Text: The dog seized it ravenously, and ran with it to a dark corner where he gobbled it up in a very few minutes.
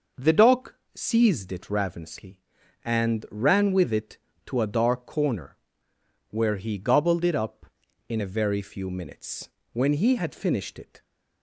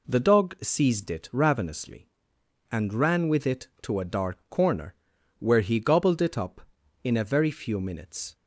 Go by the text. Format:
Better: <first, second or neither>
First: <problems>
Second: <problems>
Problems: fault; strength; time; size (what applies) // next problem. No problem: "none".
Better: second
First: pauses between "dog" and "seized"; slight; at 0.7 s; 0.22 s long // pauses between "corner" and "where"; noticeable; at 5.5 s; 0.72 s long // goes on to say "When he had finished it"; noticeable; from 9.7 s on; 1.3 s long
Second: pauses between "corner" and "where"; at 4.9 s; 0.44 s long